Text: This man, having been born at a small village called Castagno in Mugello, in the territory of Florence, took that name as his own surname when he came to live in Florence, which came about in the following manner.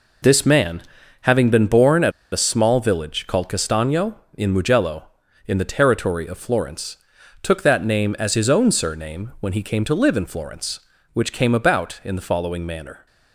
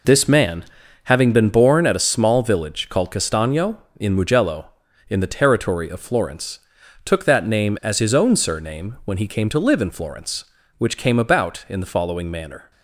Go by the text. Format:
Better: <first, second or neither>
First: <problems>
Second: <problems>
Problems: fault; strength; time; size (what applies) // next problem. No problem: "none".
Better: second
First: pauses between "at" and "a"; slight; at 2.1 s; 0.21 s long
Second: none